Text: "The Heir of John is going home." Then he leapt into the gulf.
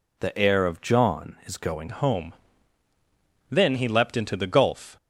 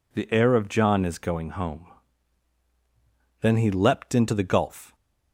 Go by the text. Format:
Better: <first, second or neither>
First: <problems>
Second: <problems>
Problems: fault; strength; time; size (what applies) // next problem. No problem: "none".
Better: second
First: changes voice at "home"; from 1.8 s on; 3.1 s long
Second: none